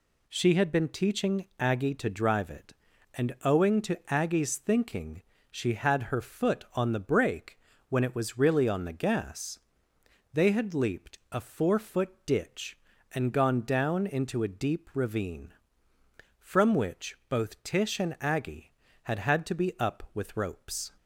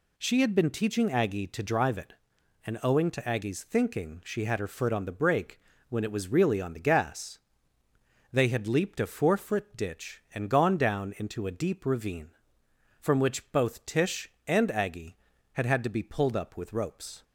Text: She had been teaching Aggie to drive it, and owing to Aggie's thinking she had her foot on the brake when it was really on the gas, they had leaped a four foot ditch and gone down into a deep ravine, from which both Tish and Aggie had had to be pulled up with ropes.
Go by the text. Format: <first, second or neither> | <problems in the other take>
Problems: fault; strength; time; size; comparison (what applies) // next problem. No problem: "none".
second | pauses between "thinking" and "she"; slight; at 5.2 s; 0.28 s long // pauses between "brake" and "when"; slight; at 7.5 s; 0.30 s long; slight in the second // pauses between "foot" and "ditch"; slight; at 12.0 s; 0.16 s long // skips "pulled"; at 19.7 s